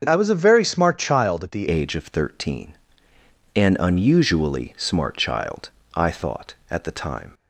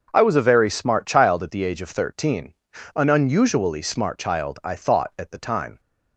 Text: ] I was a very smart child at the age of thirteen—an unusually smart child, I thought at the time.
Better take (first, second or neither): second